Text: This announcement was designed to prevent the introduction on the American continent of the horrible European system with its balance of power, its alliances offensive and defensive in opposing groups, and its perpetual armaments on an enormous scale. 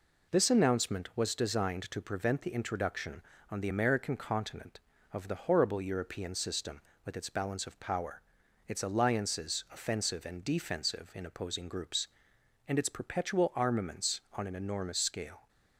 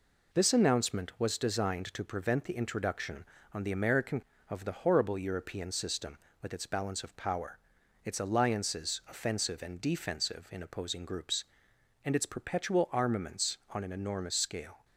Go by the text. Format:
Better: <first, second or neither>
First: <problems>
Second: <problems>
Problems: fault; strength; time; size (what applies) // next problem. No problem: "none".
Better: first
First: none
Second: skips "continent"; at 4.3 s